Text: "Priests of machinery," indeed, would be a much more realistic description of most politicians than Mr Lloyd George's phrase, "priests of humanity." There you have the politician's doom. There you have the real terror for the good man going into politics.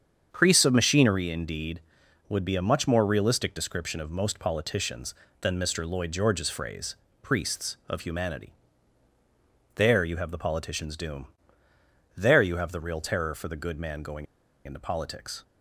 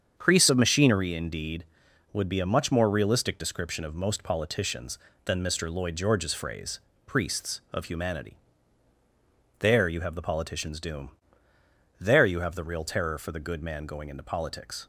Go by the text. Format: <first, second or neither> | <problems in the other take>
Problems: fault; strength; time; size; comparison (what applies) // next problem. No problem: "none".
second | starts louder than the rest; strong; until 1.3 s; 7.5 dB; strong in the second // pauses between "going" and "into"; at 14.2 s; 0.40 s long